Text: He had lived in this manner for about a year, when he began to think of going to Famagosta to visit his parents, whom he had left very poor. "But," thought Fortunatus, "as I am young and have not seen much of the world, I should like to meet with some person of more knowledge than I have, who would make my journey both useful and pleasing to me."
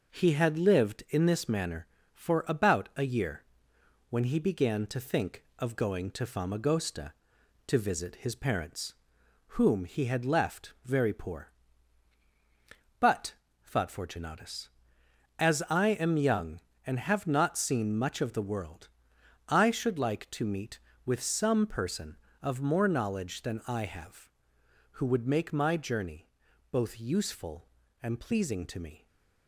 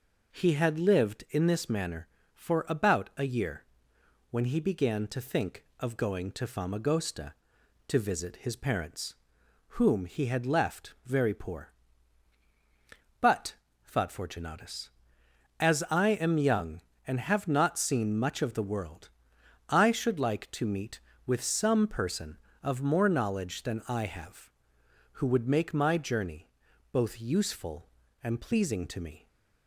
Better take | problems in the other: second | gets quieter; slight; throughout; 3 dB // pauses between "journey" and "both"; at 26.2 s; 0.42 s long; also in the second // stays silent after the last word; slight; from 28.9 s on; 0.5 s long

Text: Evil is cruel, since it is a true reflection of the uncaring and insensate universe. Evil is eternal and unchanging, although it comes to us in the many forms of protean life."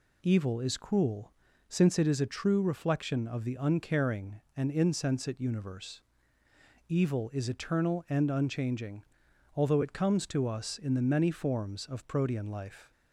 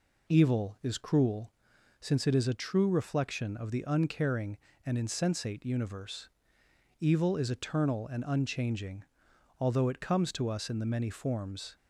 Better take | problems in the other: first | stops before "of protean life"; at 11.7 s

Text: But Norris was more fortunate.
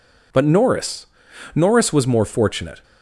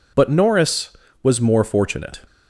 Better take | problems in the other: second | says "Norris" twice; at 1.5 s

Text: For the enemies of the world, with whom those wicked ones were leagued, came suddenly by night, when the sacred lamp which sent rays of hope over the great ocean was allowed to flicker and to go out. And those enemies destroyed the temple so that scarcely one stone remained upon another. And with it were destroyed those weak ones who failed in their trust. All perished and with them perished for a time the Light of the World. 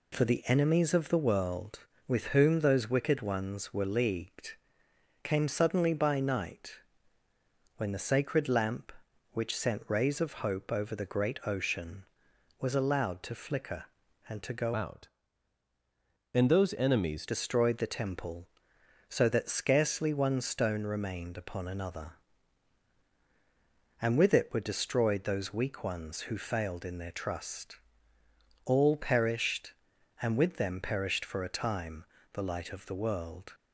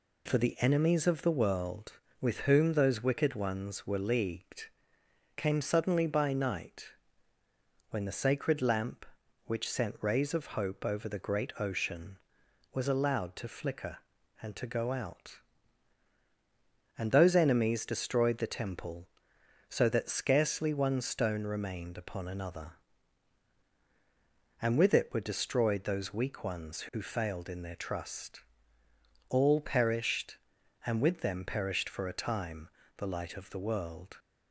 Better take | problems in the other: second | changes voice from "out" to "enemies"; from 14.7 to 17.2 s; 2.5 s long // pauses between "time" and "the"; slight; at 32.0 s; 0.30 s long; slight in the second

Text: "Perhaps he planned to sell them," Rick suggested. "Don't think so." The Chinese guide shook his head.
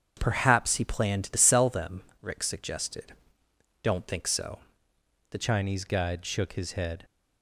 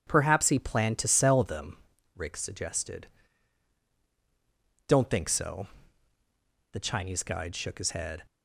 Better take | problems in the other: second | starts louder than the rest; strong; until 1.2 s; 7 dB // changes voice at "Chinese"; from 5.4 s on; 1.6 s long

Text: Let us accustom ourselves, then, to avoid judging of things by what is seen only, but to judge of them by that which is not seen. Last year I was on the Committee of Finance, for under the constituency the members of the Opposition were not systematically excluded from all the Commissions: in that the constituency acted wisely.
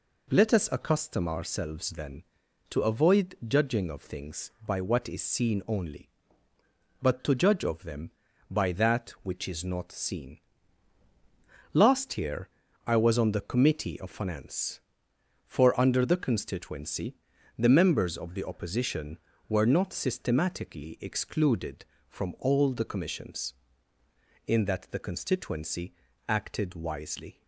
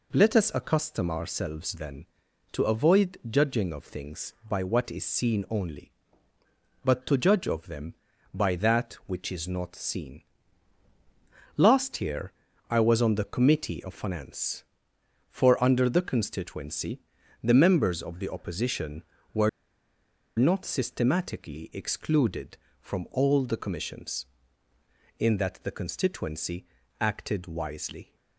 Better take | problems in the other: first | pauses between "year" and "I"; slight; at 12.3 s; 0.36 s long; slight in the first // pauses between "constituency" and "the"; at 16.9 s; 0.42 s long; also in the first // pauses between "were" and "not"; noticeable; at 19.4 s; 0.89 s long // pauses between "constituency" and "acted"; slight; at 26.6 s; 0.32 s long; slight in the first

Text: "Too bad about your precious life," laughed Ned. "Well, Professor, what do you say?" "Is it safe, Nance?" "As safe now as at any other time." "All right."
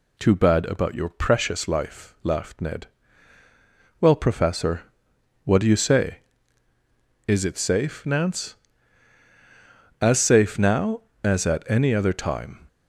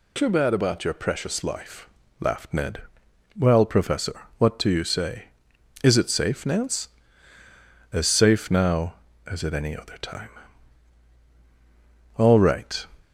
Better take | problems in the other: second | stops before "All right"; at 12.6 s

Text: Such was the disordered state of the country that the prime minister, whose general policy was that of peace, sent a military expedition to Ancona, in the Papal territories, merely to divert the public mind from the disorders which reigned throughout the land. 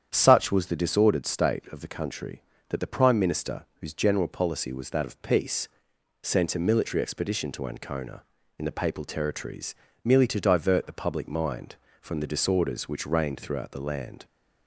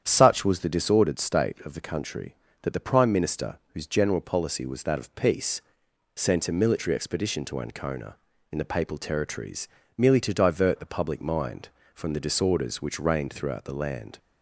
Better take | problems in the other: neither | starts louder than the rest; strong; the same in both

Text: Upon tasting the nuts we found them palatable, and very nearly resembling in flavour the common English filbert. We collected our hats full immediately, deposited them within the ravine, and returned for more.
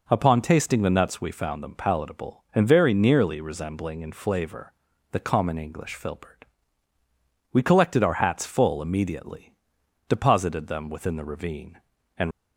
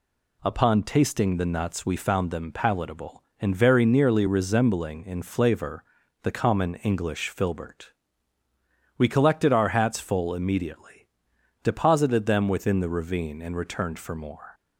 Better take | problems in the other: second | pauses between "flavour" and "the"; at 4.7 s; 0.40 s long; also in the second // stops before "returned for more"; at 12.3 s

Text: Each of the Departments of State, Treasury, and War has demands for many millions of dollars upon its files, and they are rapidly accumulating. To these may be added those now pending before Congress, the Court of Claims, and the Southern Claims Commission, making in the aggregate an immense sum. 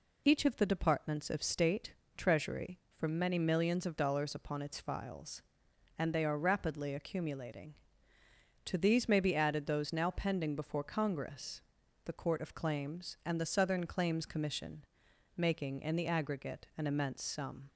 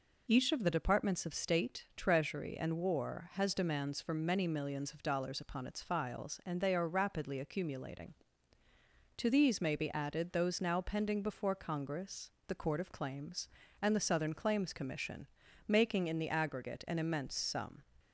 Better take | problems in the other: second | skips "and War has demands"; at 2.8 s

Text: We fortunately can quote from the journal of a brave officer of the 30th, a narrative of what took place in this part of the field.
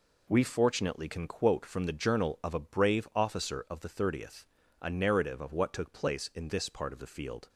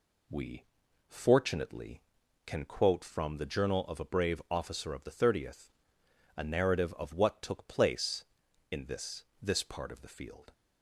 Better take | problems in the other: first | pauses between "We" and "fortunately"; at 0.6 s; 0.42 s long // says "this" twice; at 9.4 s

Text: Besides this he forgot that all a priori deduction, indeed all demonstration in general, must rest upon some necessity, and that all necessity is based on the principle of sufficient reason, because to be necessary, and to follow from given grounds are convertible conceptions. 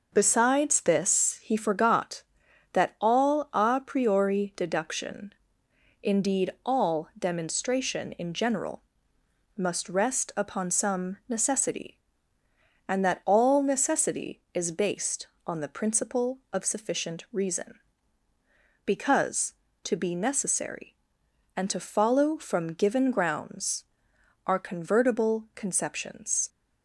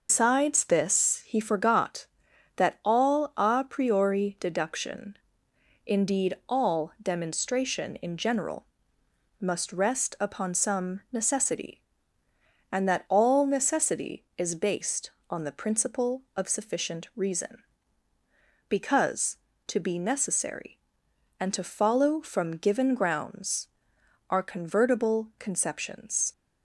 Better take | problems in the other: first | loses the start of "Besides"; at 0.0 s; 125 ms

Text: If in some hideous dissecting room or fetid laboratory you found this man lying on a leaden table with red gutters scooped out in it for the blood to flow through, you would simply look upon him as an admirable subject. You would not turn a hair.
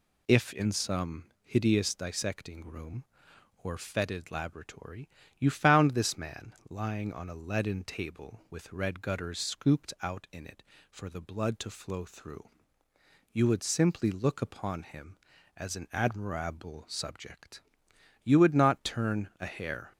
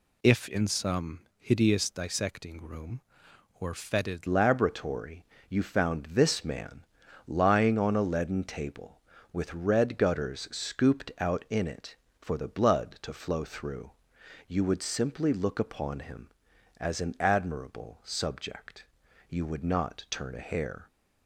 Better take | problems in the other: first | pauses between "some" and "hideous"; slight; at 1.2 s; 0.18 s long; slight in the first // changes voice at "laboratory"; from 4.2 s on; 16.6 s long // pauses between "laboratory" and "you"; slight; at 5.2 s; 0.24 s long; slight in the first // pauses between "man" and "lying"; at 6.8 s; 0.42 s long

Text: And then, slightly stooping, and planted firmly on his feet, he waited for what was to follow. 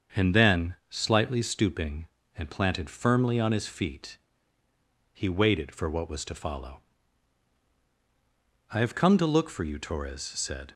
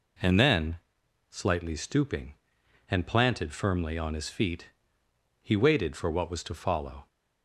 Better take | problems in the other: second | starts louder than the rest; until 1.2 s; 7 dB // goes on to say "I have come to look for you Torres said"; strong; from 8.7 s on; 2.0 s long

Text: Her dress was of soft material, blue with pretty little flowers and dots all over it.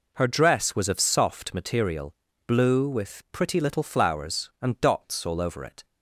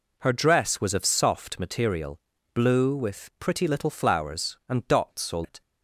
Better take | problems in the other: first | skips "over"; at 5.4 s

